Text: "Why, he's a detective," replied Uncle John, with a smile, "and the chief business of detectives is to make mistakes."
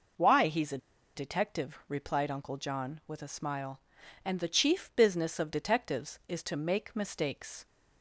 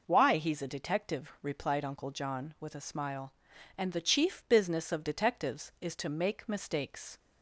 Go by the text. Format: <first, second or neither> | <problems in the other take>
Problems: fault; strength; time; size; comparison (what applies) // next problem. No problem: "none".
second | pauses between "a" and "detective"; at 0.7 s; 0.37 s long